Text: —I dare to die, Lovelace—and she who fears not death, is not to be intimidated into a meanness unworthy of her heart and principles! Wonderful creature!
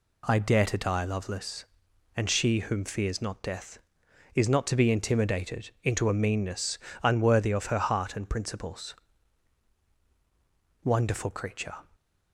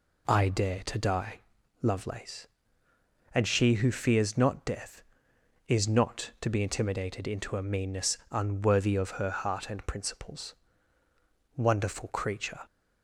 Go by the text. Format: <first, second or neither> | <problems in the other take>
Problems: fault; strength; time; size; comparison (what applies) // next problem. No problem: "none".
second | says "whom" for "who"; at 2.6 s // pauses between "meanness" and "unworthy"; slight; at 6.7 s; 0.24 s long